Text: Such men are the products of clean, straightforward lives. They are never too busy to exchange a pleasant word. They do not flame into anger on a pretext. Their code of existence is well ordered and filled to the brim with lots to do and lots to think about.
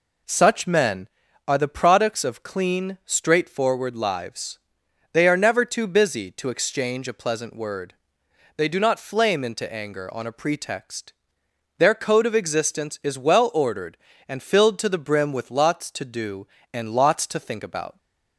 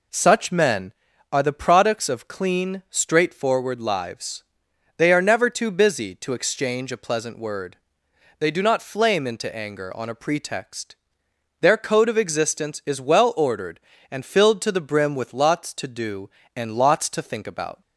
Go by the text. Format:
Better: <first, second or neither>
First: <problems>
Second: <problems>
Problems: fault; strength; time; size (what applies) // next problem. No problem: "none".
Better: neither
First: none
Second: none